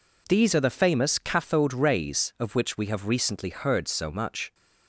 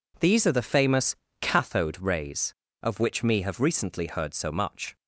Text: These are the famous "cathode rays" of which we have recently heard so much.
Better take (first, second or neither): first